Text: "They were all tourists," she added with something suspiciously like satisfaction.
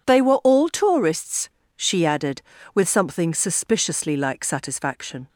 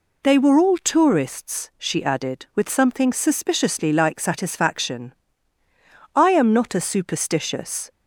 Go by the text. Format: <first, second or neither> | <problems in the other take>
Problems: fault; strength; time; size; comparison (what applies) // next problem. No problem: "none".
first | goes on to say "I am not a superstitious"; strong; from 6.1 s on; 1.7 s long